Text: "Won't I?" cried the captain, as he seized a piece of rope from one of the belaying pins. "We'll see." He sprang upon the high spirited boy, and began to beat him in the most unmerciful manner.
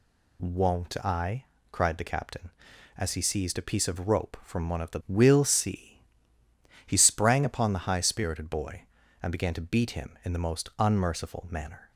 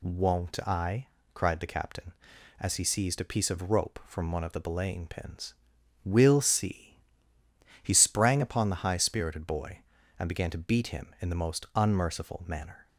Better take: second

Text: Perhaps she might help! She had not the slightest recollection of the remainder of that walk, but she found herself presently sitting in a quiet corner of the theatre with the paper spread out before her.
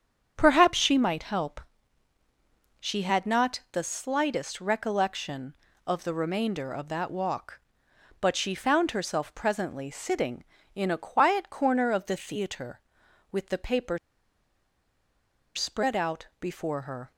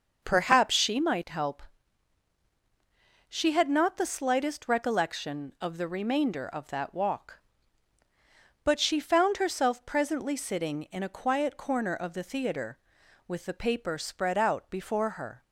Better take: second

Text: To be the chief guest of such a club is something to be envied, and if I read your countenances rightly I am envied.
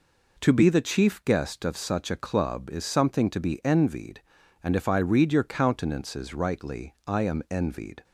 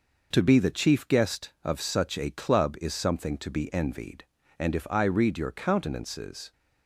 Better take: first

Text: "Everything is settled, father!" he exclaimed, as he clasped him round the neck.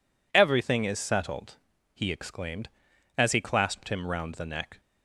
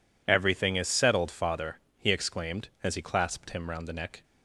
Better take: second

